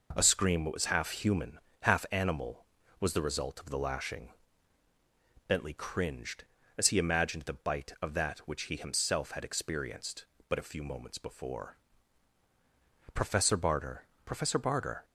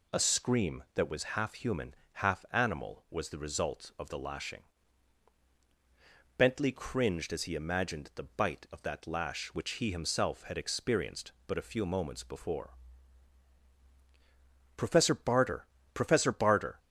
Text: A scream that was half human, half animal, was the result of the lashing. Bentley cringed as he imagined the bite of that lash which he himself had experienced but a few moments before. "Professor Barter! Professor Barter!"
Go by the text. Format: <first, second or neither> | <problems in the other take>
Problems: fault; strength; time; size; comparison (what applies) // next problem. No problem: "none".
second | skips "lash"; at 8.4 s